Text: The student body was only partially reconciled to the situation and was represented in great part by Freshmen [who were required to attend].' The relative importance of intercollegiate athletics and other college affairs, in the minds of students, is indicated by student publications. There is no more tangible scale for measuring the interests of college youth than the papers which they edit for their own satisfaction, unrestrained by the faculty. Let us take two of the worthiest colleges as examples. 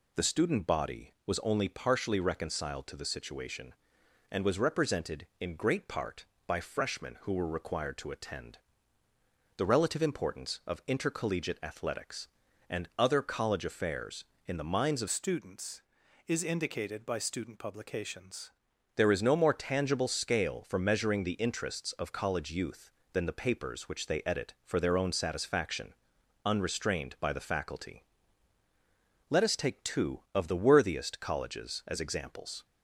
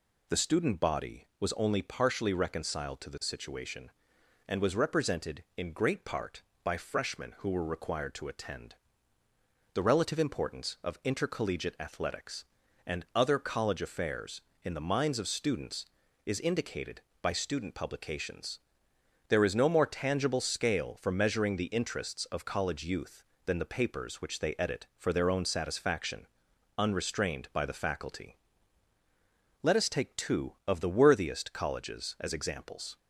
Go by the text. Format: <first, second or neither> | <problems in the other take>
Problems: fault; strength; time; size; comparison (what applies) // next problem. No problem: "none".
second | changes voice from "students" to "publications"; from 15.0 to 18.4 s; 3.4 s long